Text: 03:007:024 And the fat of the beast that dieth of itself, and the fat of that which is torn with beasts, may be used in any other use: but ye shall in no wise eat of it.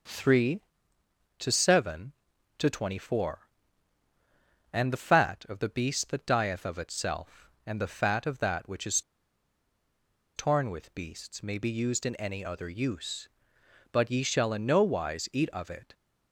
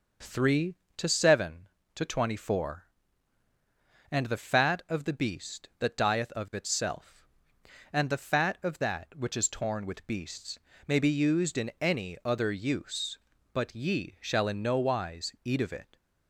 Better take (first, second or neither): second